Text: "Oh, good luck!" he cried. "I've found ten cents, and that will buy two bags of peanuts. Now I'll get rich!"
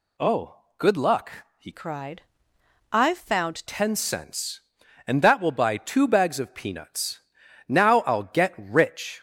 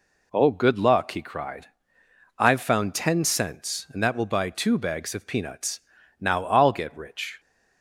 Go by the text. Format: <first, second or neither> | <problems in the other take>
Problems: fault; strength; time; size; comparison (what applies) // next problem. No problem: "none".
second | changes voice from "cried" to "found"; from 1.7 to 3.6 s; 1.9 s long